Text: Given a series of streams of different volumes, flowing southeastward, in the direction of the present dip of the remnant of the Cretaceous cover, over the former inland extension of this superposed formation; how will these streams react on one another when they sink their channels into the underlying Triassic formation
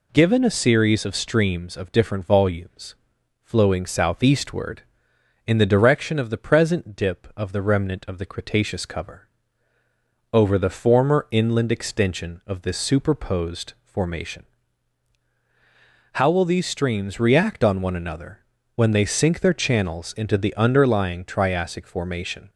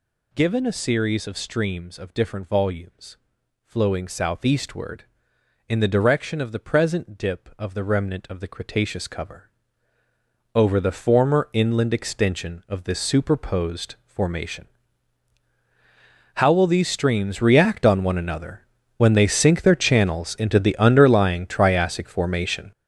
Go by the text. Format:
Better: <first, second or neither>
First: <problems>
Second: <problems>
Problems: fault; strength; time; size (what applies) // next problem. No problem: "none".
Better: first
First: pauses between "another" and "when"; slight; at 18.3 s; 0.34 s long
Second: gets louder; strong; throughout; 10 dB // pauses between "another" and "when"; slight; at 18.6 s; 0.34 s long